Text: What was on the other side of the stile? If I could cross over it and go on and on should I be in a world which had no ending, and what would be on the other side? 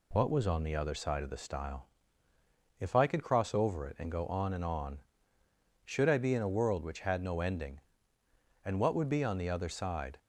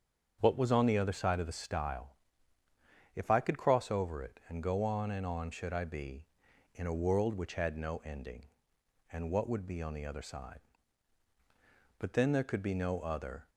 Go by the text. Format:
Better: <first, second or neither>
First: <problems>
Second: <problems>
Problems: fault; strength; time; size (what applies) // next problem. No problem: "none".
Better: first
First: none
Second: starts louder than the rest; strong; until 1.4 s; 7.5 dB // goes on to say "But then there could be no other"; from 11.9 s on; 1.5 s long